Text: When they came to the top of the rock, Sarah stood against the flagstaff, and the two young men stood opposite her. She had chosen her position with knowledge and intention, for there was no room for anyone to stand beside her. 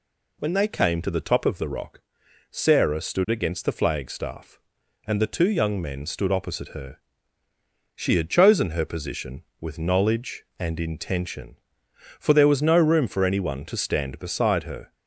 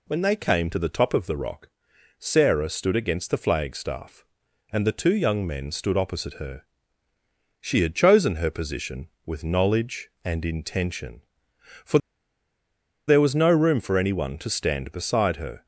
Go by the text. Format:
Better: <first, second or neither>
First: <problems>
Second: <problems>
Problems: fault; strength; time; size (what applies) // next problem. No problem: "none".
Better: first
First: none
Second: pauses between "for" and "there"; at 11.9 s; 1.1 s long